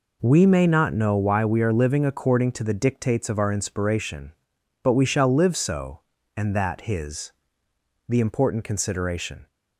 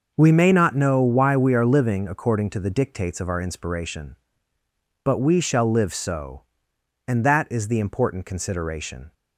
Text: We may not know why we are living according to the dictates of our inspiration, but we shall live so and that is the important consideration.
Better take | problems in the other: second | says "his" for "is"; at 6.8 s

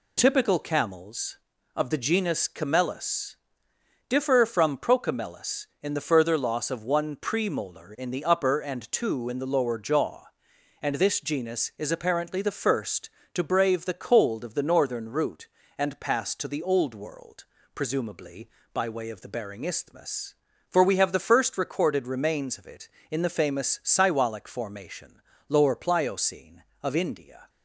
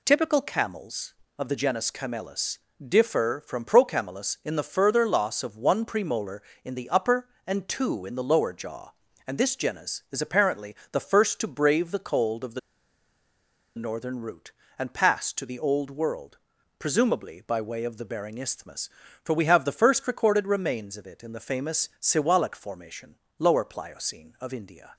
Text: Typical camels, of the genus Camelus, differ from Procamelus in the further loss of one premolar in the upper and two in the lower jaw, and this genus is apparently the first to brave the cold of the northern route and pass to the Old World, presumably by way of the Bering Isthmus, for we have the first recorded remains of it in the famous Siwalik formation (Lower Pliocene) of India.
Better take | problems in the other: first | pauses between "apparently" and "the"; slight; at 10.7 s; 0.16 s long // pauses between "the" and "northern"; at 12.5 s; 1.1 s long

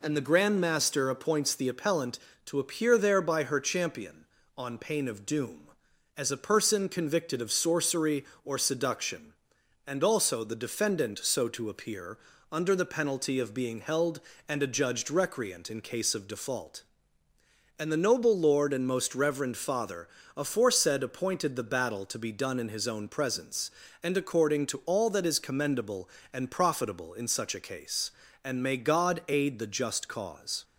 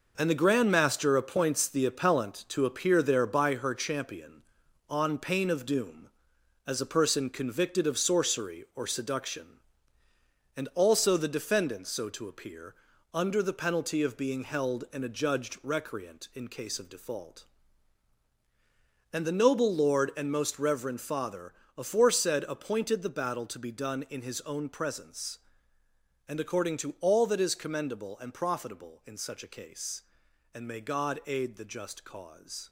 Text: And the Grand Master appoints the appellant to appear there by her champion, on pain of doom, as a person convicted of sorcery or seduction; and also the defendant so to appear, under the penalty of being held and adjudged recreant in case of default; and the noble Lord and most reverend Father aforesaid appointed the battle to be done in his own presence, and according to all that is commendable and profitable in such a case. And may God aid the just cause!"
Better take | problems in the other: first | gets quieter; strong; throughout; 8 dB // pauses between "Father" and "aforesaid"; slight; at 21.5 s; 0.24 s long; slight in the first

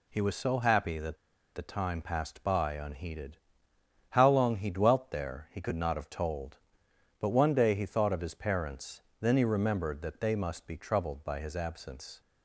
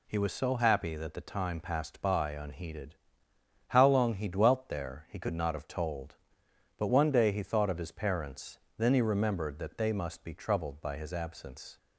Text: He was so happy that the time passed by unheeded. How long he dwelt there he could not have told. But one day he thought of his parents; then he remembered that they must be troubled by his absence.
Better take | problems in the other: second | pauses between "that" and "the"; at 1.1 s; 0.39 s long

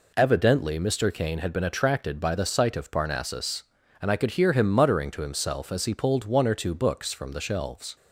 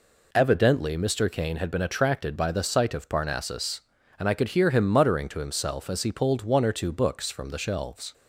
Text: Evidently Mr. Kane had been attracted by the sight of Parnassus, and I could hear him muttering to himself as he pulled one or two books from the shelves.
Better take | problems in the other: neither | none

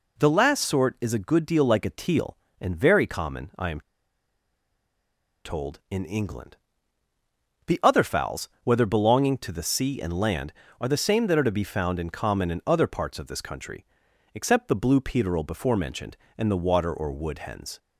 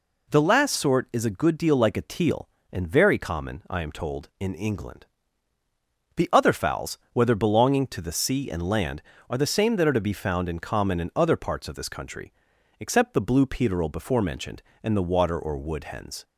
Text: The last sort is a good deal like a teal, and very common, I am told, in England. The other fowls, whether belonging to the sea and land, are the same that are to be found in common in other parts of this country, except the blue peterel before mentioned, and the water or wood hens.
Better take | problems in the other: second | pauses between "am" and "told"; strong; at 3.7 s; 1.6 s long

